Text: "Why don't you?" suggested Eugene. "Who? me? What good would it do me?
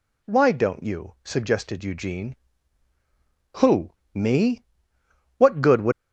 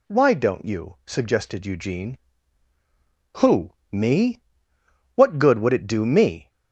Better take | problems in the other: second | stops before "it do me"; at 5.9 s

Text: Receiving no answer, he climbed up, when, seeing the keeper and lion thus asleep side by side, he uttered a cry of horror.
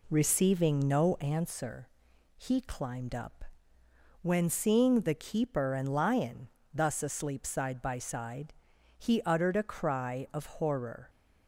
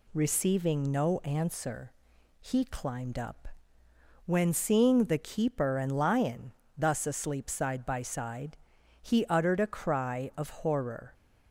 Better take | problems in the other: second | starts louder than the rest; slight; until 1.4 s; 2.5 dB // pauses between "lion" and "thus"; slight; at 6.4 s; 0.26 s long; slight in the second

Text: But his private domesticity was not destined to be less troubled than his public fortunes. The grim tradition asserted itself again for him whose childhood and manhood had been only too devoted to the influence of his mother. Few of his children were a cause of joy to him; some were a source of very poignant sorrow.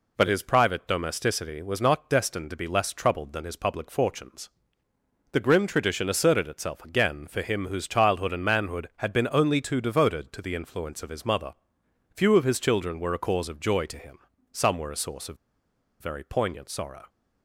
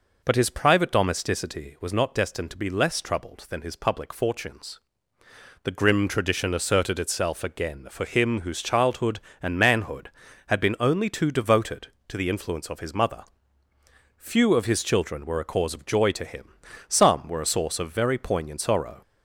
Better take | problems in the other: second | pauses between "of" and "very"; noticeable; at 15.3 s; 0.64 s long

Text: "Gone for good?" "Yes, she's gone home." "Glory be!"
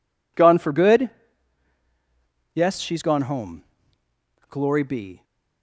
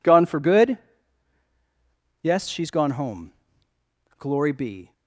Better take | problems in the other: neither | none

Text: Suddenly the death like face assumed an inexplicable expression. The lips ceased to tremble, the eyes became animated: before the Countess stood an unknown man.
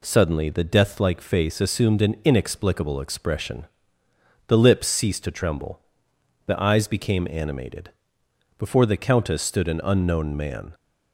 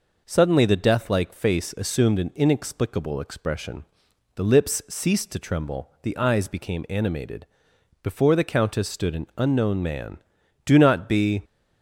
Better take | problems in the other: first | goes on to say "Do not be"; noticeable; from 10.6 s on; 0.78 s long

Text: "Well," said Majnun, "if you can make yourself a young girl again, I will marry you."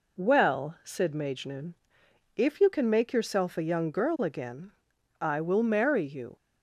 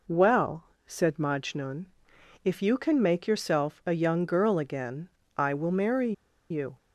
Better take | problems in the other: first | pauses between "marry" and "you"; at 6.1 s; 0.38 s long

